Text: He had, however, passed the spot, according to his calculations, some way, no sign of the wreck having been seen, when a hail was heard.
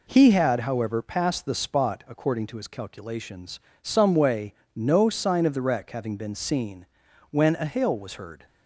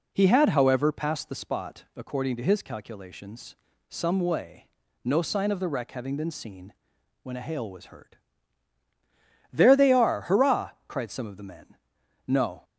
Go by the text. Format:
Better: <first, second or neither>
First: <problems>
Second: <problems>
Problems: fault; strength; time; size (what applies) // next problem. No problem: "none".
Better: first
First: none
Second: goes on to say "There they are hurrah cried some of the men No"; strong; from 9.5 s on; 3.1 s long